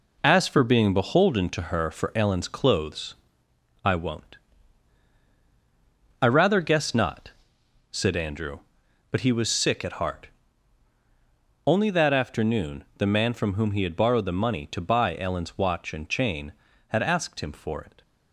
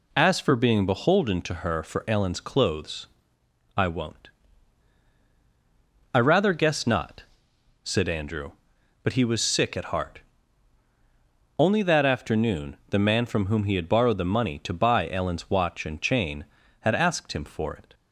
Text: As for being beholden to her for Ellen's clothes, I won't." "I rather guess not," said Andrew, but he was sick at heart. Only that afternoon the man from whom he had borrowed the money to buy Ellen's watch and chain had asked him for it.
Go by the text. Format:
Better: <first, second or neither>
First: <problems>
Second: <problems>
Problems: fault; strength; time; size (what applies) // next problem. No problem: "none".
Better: second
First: gets quieter; throughout; 6.5 dB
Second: none